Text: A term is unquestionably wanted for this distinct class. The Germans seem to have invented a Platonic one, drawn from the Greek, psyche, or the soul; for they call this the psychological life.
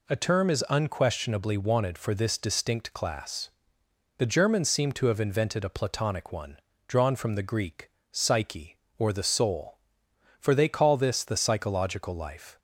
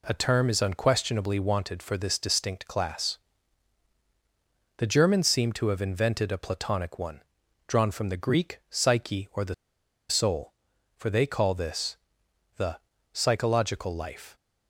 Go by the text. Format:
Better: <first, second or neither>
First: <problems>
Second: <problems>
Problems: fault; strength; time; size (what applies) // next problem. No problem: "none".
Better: first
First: none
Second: pauses between "the" and "soul"; noticeable; at 9.5 s; 0.54 s long // pauses between "this" and "the"; noticeable; at 11.9 s; 0.62 s long // pauses between "the" and "psychological"; slight; at 12.7 s; 0.36 s long